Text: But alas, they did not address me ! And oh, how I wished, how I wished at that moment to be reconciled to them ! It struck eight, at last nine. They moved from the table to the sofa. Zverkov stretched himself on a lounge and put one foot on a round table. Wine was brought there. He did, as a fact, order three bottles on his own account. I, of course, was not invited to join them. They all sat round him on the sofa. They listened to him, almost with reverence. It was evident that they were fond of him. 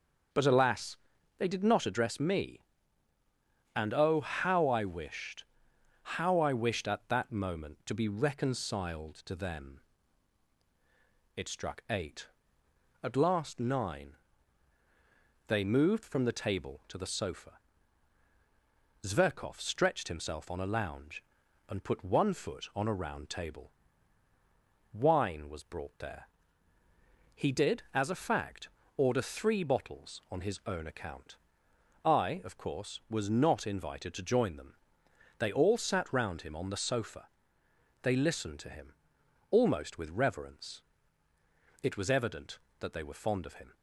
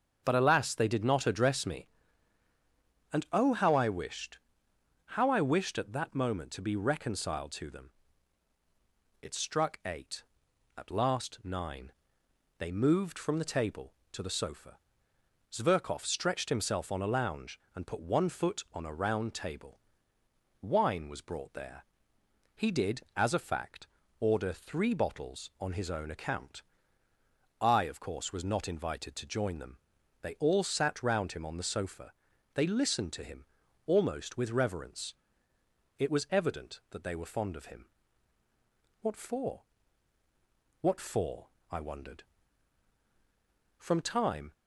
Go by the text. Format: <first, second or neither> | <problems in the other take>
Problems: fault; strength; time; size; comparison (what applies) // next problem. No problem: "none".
first | starts louder than the rest; until 1.2 s; 7 dB; also in the first // goes on to say "What for What for I wondered From time"; strong; from 39.0 s on; 5.5 s long